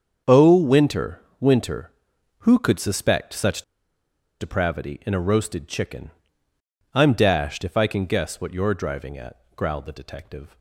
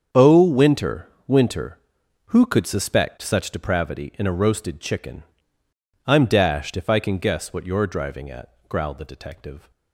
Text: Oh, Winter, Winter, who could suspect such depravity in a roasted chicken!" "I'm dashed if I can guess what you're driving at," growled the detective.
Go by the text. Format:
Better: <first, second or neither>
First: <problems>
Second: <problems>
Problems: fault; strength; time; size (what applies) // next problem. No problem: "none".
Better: second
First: starts louder than the rest; strong; until 1.4 s; 7 dB // pauses between "such" and "depravity"; noticeable; at 3.6 s; 0.78 s long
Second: starts louder than the rest; strong; until 1.3 s; 7 dB